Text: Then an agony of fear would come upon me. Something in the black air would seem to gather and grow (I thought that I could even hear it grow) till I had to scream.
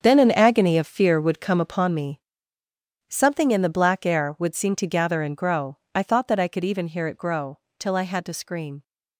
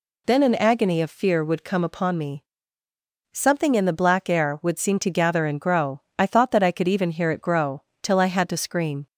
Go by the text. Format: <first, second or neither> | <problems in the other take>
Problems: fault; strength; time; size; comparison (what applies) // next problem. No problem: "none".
second | gets quieter; strong; throughout; 12 dB